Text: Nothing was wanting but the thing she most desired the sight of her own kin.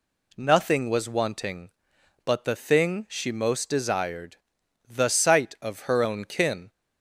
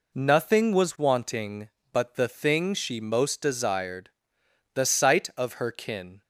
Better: first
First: pauses between "desired" and "the"; noticeable; at 4.3 s; 0.50 s long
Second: pauses between "desired" and "the"; noticeable; at 4.0 s; 0.66 s long // skips "own"; at 5.7 s

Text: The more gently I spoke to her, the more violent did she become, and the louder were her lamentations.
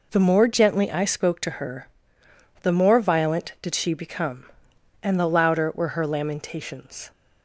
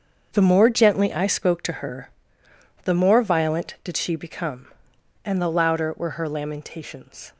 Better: first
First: none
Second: gets quieter; strong; throughout; 11 dB

